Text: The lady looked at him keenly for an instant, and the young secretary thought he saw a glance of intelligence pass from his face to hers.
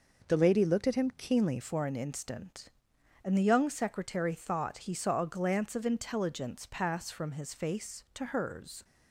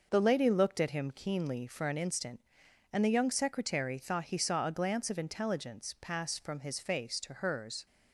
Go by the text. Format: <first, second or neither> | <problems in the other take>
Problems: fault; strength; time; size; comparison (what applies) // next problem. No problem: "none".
second | changes voice at "for"; from 1.6 s on; 7.2 s long